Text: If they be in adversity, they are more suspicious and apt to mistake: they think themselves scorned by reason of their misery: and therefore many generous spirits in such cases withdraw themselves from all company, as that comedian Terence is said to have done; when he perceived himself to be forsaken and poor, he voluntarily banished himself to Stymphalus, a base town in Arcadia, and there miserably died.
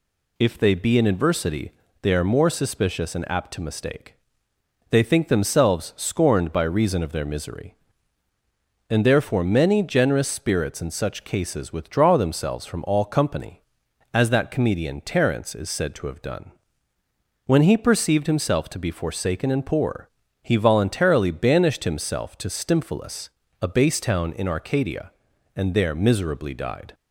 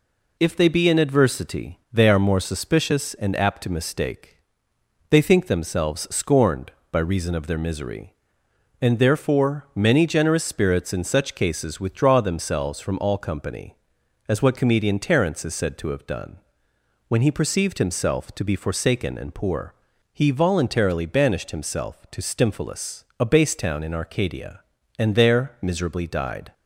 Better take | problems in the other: first | says "what" for "that"; at 14.4 s

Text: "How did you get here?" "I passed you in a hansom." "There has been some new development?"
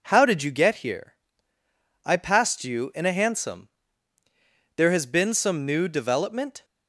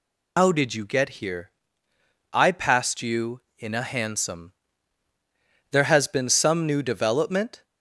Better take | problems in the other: first | loses the start of "How"; at 0.3 s; 145 ms

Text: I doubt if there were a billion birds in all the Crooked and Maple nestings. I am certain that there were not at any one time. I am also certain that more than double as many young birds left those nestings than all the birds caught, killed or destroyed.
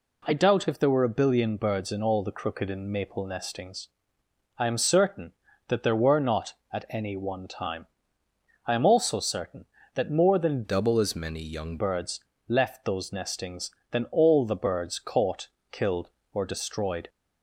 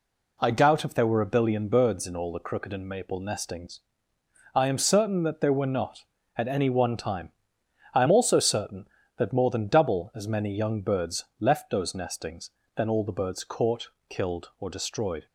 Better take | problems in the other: second | changes voice from "double" to "young"; from 10.6 to 11.7 s; 1.1 s long // pauses between "birds" and "left"; slight; at 12.1 s; 0.30 s long; slight in the second

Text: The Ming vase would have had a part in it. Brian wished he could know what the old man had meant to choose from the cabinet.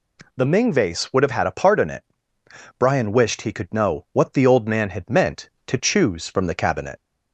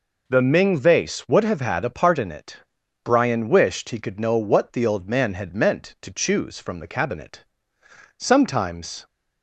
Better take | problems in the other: first | goes on to say "Sometimes"; noticeable; from 8.1 s on; 0.88 s long

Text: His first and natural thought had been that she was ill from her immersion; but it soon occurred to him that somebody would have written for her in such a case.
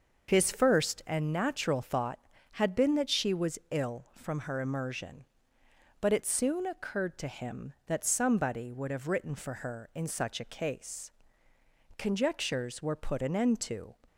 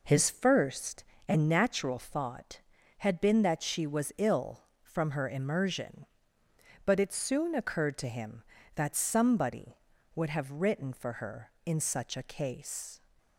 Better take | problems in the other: second | starts louder than the rest; noticeable; until 1.3 s; 6 dB // goes on to say "Conjectures were put an end to"; strong; from 11.9 s on; 1.9 s long

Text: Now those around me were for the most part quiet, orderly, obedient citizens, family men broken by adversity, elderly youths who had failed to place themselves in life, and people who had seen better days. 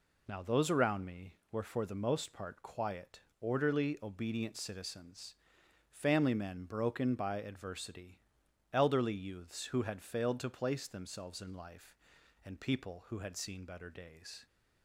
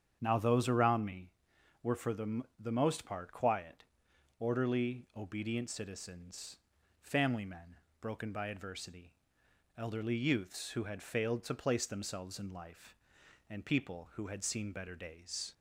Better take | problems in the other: first | starts louder than the rest; strong; until 1.2 s; 8 dB // says "the" twice; at 2.5 s // pauses between "men" and "broken"; slight; at 7.7 s; 0.24 s long

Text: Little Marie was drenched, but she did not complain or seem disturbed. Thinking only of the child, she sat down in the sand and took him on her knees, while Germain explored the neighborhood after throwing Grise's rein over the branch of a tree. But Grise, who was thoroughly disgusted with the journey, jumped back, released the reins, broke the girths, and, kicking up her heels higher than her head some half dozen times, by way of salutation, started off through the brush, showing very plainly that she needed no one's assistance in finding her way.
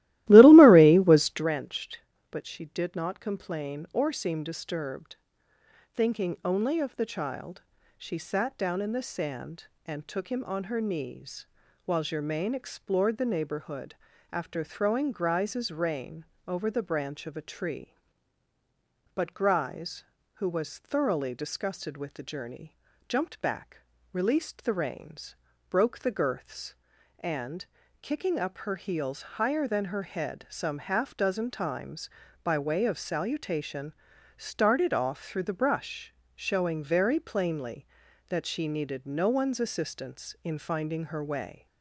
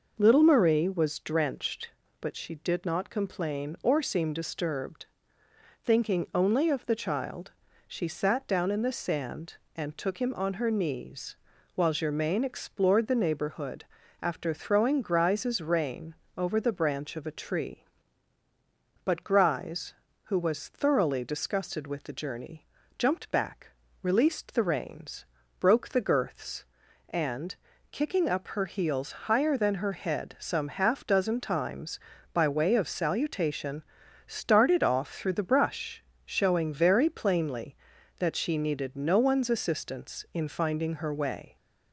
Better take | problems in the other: second | starts louder than the rest; strong; until 1.5 s; 17 dB // pauses between "neighborhood" and "after"; slight; at 13.9 s; 0.36 s long; slight in the second // pauses between "rein" and "over"; slight; at 16.2 s; 0.24 s long; slight in the second

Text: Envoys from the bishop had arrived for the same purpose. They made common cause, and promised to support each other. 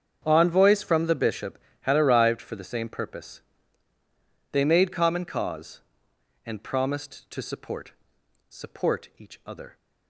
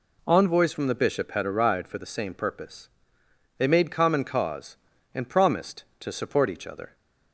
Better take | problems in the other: second | starts louder than the rest; strong; until 1.2 s; 7.5 dB // says "support" twice; at 8.4 s

